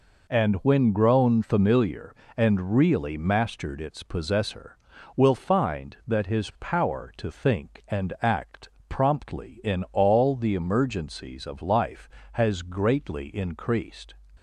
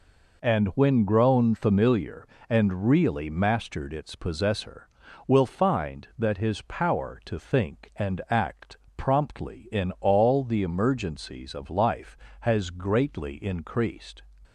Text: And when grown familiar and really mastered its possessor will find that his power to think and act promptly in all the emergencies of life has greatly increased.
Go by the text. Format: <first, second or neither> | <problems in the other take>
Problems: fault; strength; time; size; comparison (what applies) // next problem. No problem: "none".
neither | pauses between "act" and "promptly"; slight; the same in both